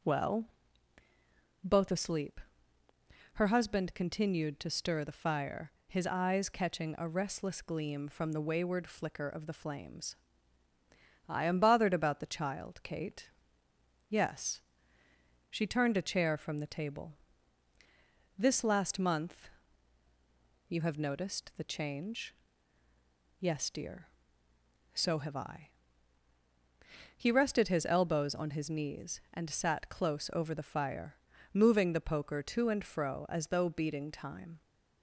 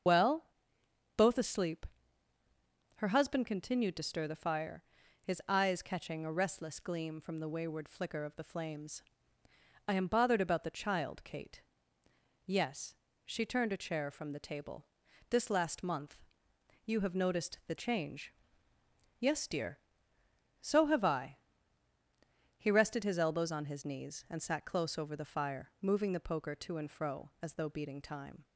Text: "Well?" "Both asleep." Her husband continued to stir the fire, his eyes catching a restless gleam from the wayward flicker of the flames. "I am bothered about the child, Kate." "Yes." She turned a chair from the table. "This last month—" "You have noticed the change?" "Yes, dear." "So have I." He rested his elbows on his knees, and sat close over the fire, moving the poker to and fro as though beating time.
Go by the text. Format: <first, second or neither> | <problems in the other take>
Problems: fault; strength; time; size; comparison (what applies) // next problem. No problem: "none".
first | loses the start of "Well"; at 0.0 s; 60 ms // starts louder than the rest; until 1.7 s; 6.5 dB